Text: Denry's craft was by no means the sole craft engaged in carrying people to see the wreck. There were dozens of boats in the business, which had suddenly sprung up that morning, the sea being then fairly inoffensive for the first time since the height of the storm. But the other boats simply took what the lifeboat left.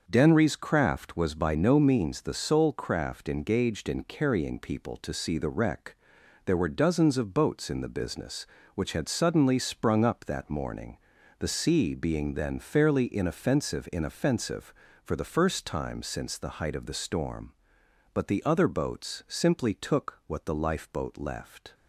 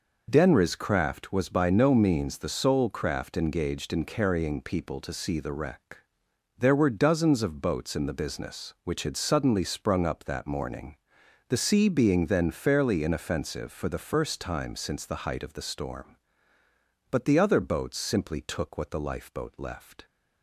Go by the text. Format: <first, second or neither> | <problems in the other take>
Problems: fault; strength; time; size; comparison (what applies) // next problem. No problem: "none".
second | starts louder than the rest; until 1.0 s; 6.5 dB // says "inoffensive" twice; at 13.9 s